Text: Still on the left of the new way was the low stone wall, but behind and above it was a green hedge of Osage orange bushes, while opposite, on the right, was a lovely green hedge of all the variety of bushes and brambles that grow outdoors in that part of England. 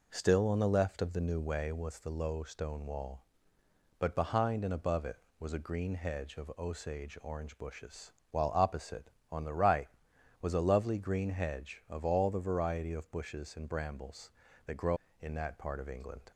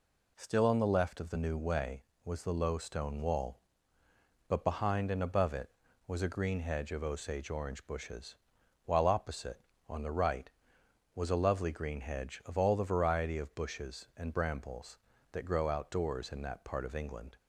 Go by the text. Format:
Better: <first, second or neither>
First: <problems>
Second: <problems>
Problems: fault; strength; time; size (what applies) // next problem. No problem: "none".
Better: second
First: skips "outdoors"; at 15.0 s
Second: none